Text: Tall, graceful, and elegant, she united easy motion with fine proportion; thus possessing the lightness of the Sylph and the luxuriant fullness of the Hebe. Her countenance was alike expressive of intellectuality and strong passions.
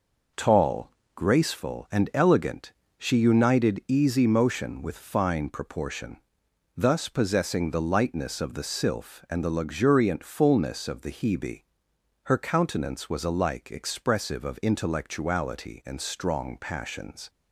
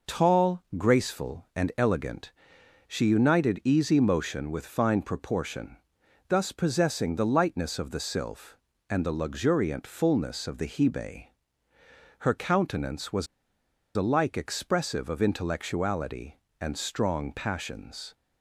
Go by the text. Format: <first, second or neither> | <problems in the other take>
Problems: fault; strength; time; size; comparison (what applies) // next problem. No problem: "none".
first | pauses between "was" and "alike"; noticeable; at 13.2 s; 0.70 s long